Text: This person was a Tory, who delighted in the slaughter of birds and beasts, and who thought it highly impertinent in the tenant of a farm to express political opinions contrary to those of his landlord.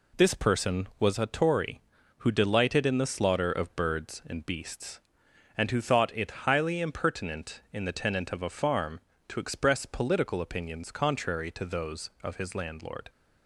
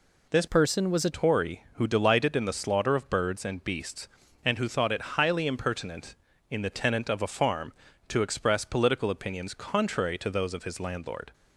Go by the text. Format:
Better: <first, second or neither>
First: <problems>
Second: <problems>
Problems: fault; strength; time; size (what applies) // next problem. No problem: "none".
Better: first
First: none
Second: changes voice from "person" to "a"; from 0.4 to 1.1 s; 0.7 s long